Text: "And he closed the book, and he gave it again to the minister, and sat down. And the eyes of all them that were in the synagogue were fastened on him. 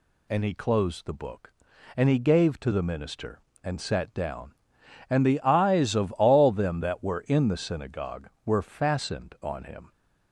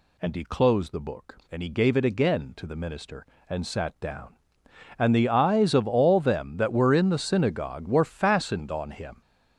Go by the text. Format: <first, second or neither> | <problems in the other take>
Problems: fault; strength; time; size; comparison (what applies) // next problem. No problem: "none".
second | skips "it again"; at 2.5 s